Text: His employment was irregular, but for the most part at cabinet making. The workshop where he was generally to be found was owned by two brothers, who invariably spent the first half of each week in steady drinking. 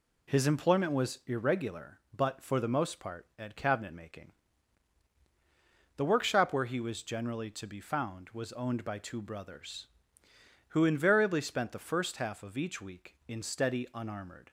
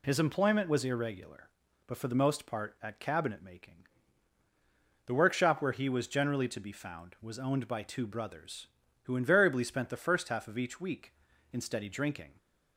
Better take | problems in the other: second | says "unarmored" for "drinking"; at 13.9 s

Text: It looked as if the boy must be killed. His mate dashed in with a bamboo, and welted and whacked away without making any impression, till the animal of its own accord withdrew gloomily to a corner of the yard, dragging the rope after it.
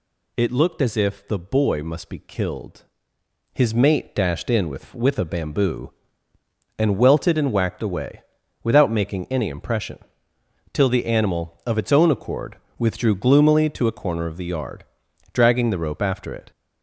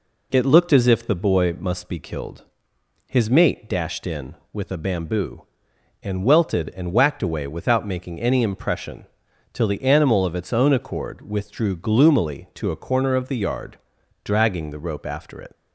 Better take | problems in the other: second | says "with" twice; at 4.9 s // pauses between "away" and "without"; at 8.2 s; 0.42 s long // pauses between "accord" and "withdrew"; slight; at 12.5 s; 0.22 s long

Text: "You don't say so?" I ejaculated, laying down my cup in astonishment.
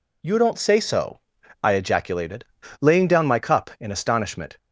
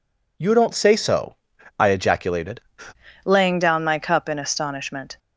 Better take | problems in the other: first | changes voice at "laying"; from 3.2 s on; 1.9 s long

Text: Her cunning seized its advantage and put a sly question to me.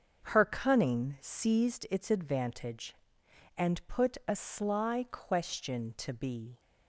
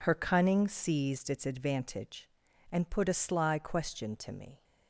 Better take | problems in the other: second | starts louder than the rest; noticeable; until 1.3 s; 6 dB // says "be" for "me"; at 6.1 s

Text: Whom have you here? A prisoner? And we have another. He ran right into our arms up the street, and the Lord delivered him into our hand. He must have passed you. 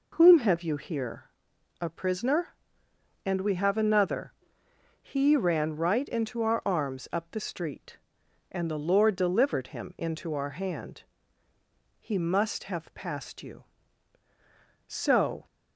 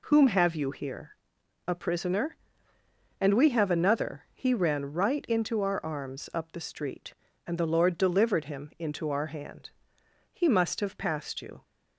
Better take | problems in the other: second | goes on to say "So"; from 14.8 s on; 0.58 s long

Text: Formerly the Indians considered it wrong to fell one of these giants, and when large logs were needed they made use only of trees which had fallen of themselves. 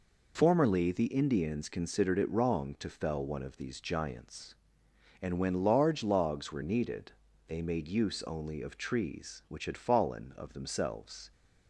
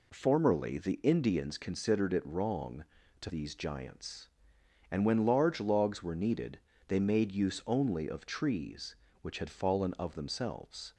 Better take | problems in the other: first | skips "fell one of"; at 3.2 s // pauses between "needed" and "they"; slight; at 6.5 s; 0.30 s long; slight in the first

